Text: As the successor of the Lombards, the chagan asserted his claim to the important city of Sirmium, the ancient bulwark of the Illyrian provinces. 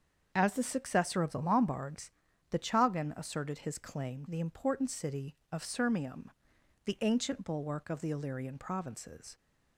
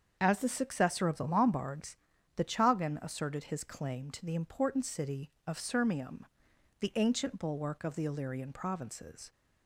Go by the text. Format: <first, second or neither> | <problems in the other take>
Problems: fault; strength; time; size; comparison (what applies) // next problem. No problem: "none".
second | starts louder than the rest; until 1.3 s; 7 dB; strong in the second // skips "to"; at 4.2 s